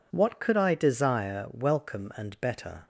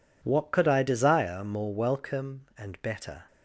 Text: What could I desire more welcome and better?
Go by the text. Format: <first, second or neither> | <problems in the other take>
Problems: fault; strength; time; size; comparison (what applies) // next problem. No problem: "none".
second | skips "more"; at 1.4 s